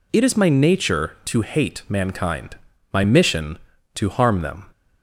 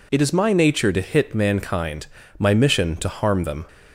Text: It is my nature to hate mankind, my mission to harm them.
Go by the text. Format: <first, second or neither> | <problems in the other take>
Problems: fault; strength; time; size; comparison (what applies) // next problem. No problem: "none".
first | says "hit" for "hate"; at 1.0 s